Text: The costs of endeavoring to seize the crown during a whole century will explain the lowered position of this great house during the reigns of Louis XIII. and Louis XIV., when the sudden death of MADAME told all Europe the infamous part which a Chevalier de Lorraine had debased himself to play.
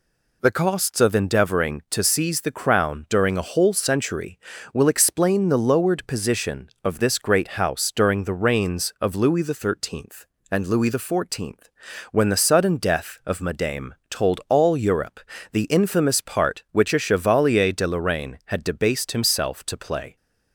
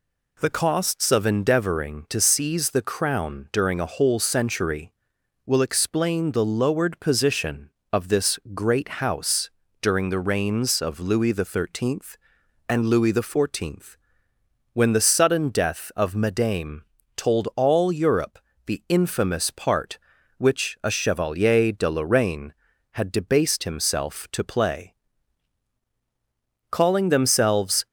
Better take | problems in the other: first | pauses between "this" and "great"; slight; at 8.3 s; 0.16 s long // pauses between "house" and "during"; slight; at 9.4 s; 0.32 s long // pauses between "MADAME" and "told"; slight; at 16.8 s; 0.32 s long // pauses between "Europe" and "the"; slight; at 18.3 s; 0.28 s long; slight in the first // goes on to say "Calling themselves"; noticeable; from 26.6 s on; 1.1 s long

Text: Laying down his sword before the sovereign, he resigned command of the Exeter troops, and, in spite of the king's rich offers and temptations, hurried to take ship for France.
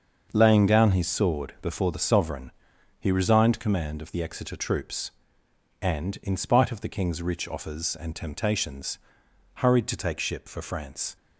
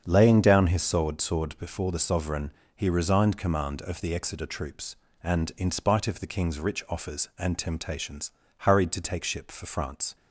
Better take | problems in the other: first | starts louder than the rest; strong; until 1.0 s; 7.5 dB; also in the first // says "sword" twice; at 1.2 s

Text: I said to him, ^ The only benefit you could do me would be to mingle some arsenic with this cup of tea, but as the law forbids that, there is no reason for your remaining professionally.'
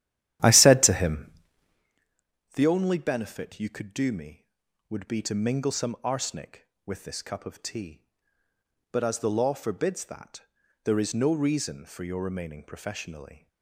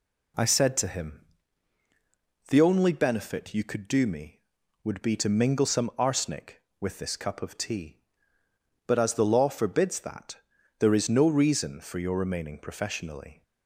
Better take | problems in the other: second | starts louder than the rest; strong; until 2.0 s; 12 dB

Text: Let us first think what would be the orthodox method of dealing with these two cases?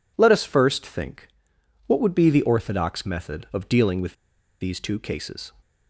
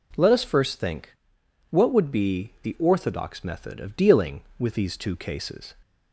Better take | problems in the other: second | pauses between "think" and "what"; noticeable; at 1.2 s; 0.62 s long; noticeable in the second // pauses between "with" and "these"; noticeable; at 4.1 s; 0.47 s long

